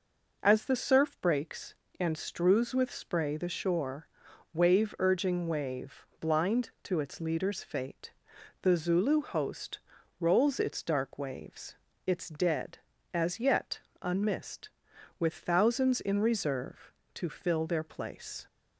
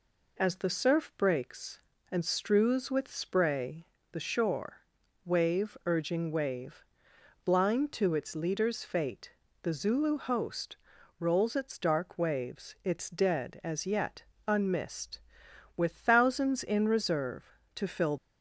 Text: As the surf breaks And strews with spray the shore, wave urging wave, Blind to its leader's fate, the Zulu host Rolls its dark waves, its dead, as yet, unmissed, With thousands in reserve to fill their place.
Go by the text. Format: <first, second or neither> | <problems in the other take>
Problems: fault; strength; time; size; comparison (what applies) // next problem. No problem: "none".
first | pauses between "spray" and "the"; slight; at 3.8 s; 0.24 s long // pauses between "host" and "Rolls"; at 10.7 s; 0.42 s long; also in the first // stops before "their place"; at 18.1 s